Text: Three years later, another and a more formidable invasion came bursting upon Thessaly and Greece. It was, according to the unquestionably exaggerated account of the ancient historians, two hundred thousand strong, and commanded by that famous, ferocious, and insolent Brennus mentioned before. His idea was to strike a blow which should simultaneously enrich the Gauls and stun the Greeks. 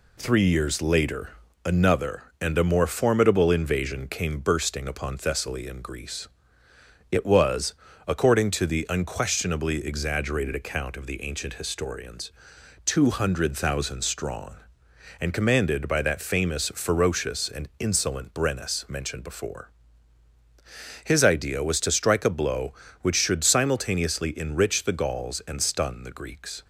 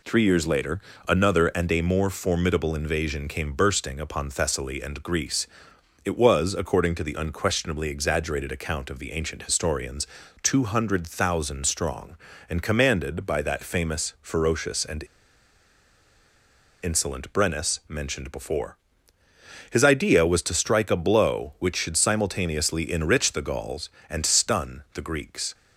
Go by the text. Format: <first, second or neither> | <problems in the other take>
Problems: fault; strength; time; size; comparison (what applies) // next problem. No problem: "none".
first | pauses between "and" and "insolent"; strong; at 15.0 s; 1.7 s long